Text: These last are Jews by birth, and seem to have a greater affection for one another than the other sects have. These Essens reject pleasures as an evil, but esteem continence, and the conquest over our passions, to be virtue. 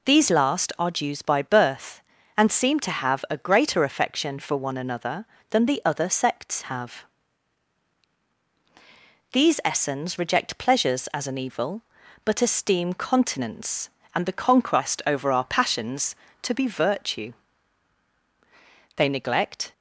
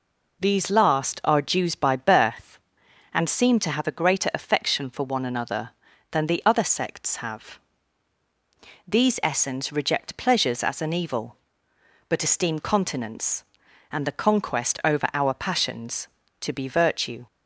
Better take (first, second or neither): second